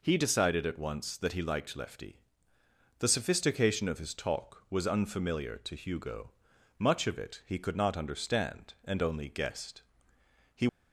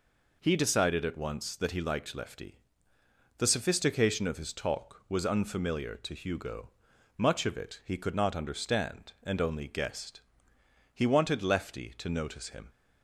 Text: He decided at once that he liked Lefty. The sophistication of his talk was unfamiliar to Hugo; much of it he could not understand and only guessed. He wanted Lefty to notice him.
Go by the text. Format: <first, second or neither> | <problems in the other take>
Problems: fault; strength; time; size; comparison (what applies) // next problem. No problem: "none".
second | stops before "wanted Lefty to notice him"; at 10.6 s